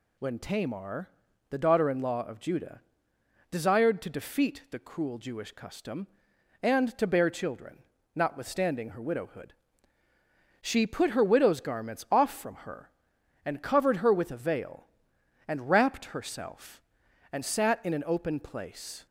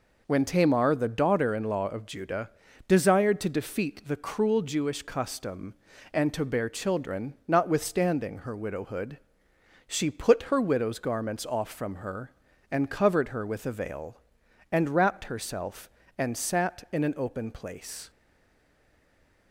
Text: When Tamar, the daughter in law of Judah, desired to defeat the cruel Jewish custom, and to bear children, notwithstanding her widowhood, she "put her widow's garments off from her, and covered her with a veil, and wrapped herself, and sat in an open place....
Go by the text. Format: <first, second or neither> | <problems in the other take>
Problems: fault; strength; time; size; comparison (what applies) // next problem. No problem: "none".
first | stays silent after the last word; noticeable; from 18.1 s on; 1.4 s long